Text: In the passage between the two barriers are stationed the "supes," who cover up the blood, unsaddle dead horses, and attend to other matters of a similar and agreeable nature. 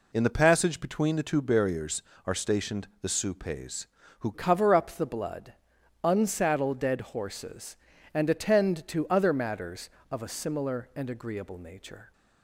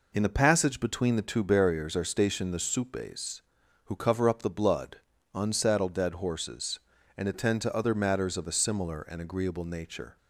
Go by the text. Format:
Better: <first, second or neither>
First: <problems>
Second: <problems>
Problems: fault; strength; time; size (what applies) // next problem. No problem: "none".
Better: second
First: changes voice at "cover"; from 4.3 s on; 7.8 s long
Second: none